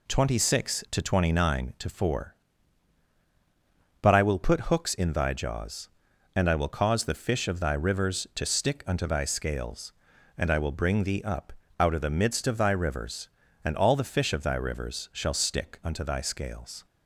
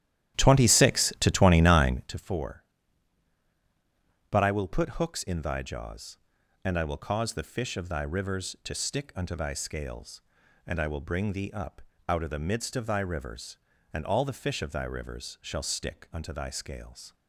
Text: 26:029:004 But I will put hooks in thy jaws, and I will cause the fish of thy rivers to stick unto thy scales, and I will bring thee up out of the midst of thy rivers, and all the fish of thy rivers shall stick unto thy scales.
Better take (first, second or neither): first